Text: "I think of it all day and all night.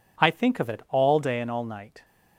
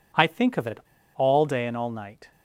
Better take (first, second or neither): first